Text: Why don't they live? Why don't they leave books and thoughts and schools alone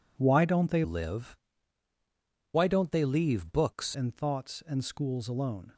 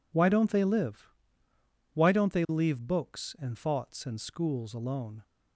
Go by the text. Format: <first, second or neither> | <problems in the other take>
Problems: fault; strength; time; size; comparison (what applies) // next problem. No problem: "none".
second | changes voice from "live" to "books"; from 0.8 to 3.9 s; 3.1 s long